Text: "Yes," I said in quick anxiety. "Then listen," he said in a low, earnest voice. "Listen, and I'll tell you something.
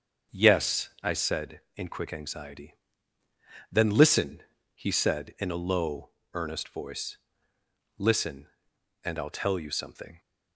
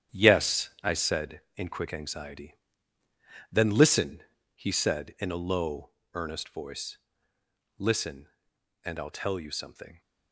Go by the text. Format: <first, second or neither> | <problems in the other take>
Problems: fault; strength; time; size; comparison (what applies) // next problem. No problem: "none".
first | gets quieter; strong; throughout; 8.5 dB // starts louder than the rest; strong; until 1.2 s; 9.5 dB; also in the first